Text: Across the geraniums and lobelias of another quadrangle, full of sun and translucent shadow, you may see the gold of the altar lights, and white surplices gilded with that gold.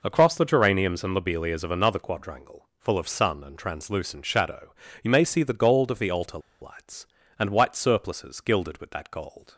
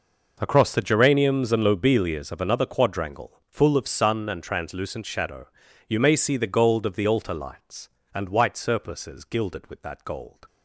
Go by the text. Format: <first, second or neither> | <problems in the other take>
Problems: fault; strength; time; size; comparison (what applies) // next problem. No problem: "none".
second | pauses between "altar" and "lights"; slight; at 6.3 s; 0.21 s long